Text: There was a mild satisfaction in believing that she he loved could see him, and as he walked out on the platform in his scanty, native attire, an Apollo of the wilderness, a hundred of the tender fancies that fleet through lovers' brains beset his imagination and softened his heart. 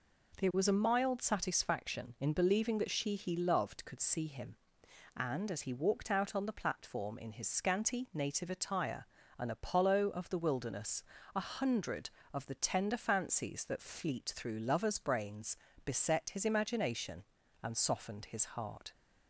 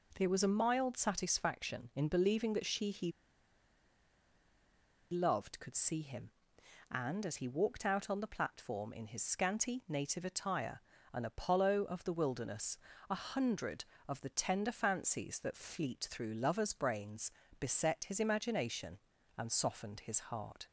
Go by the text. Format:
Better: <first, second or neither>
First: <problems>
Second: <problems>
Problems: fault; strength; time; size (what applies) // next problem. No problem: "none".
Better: first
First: pauses between "brains" and "beset"; slight; at 15.5 s; 0.30 s long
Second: pauses between "he" and "loved"; strong; at 3.1 s; 1.9 s long // pauses between "brains" and "beset"; slight; at 17.3 s; 0.30 s long